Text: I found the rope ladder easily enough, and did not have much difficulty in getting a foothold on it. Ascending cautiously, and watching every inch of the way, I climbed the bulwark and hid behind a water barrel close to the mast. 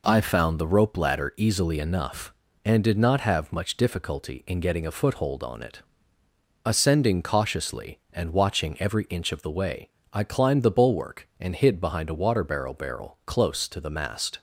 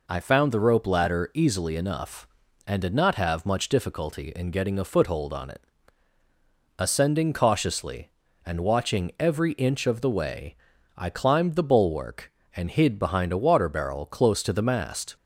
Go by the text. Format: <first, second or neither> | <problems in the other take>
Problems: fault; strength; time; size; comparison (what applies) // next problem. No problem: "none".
second | says "barrel" twice; at 12.7 s